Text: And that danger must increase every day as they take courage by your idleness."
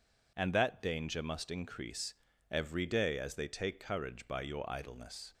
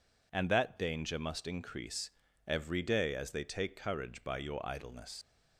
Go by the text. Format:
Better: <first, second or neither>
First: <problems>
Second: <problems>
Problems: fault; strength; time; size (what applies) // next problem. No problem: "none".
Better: first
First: pauses between "increase" and "every"; slight; at 2.1 s; 0.34 s long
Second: pauses between "increase" and "every"; slight; at 2.1 s; 0.34 s long // leaves "idleness" unfinished; at 5.2 s; 80 ms